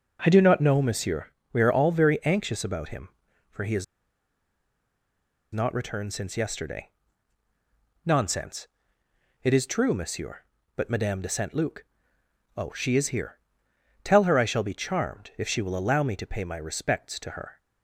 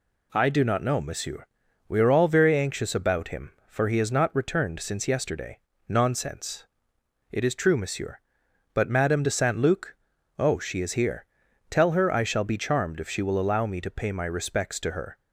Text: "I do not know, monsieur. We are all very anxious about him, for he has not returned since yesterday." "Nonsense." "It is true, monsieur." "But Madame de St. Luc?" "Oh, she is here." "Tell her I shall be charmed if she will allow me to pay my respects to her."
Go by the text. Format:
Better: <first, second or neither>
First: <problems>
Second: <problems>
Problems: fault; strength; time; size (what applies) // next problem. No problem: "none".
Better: second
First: pauses between "has" and "not"; strong; at 3.8 s; 1.6 s long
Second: none